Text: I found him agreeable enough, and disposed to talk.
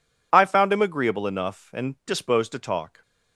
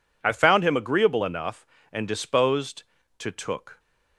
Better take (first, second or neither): first